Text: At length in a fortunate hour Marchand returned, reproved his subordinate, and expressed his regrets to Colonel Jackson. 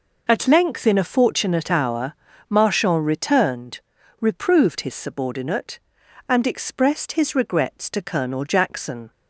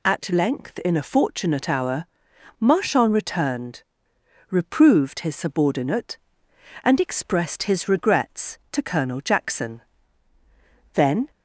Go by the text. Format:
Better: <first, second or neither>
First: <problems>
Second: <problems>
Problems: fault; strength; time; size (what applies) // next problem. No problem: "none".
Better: first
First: pauses between "hour" and "Marchand"; slight; at 2.1 s; 0.36 s long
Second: pauses between "hour" and "Marchand"; noticeable; at 2.0 s; 0.52 s long // goes on to say "Then"; slight; from 10.9 s on; 0.36 s long